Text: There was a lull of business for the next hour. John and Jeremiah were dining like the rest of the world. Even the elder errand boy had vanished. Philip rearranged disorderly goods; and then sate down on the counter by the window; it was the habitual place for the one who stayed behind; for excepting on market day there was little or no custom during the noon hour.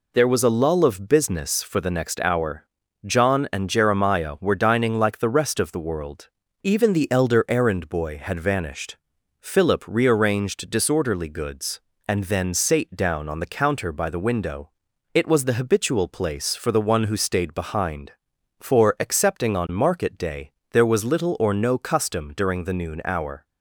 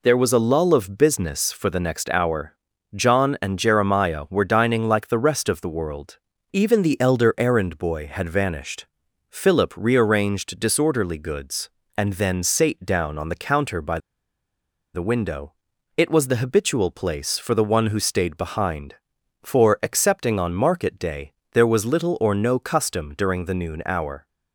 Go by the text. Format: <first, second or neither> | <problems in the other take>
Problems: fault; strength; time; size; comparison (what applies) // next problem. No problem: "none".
first | pauses between "by" and "the"; noticeable; at 13.9 s; 0.95 s long // pauses between "day" and "there"; slight; at 21.3 s; 0.20 s long; slight in the first